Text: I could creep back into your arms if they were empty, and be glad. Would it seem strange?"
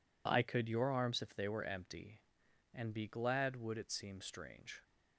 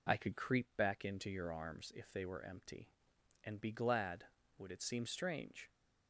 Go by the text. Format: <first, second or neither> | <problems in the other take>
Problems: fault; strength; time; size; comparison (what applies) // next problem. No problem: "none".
second | skips "creep back into"; at 0.6 s